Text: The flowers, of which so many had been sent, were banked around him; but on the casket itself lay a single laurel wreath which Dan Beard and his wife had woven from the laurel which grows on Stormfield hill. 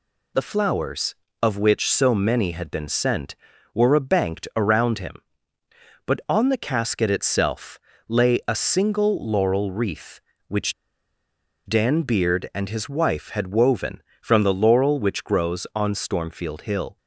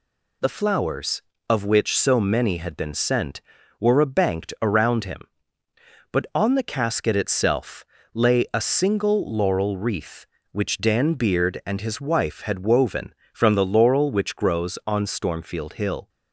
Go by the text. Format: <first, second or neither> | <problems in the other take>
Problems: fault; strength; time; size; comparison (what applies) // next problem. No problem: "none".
second | pauses between "itself" and "lay"; slight; at 7.7 s; 0.28 s long; slight in the second // pauses between "which" and "Dan"; noticeable; at 10.7 s; 0.93 s long